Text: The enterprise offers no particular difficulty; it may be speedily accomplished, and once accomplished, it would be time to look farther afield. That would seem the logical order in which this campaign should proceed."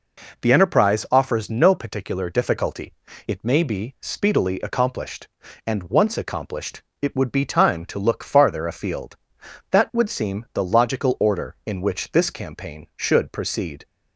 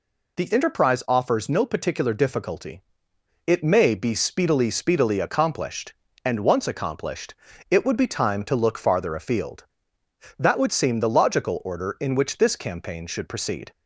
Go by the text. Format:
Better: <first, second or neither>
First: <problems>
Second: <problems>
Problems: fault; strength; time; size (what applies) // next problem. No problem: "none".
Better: first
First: none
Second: says "speedily" twice; at 4.6 s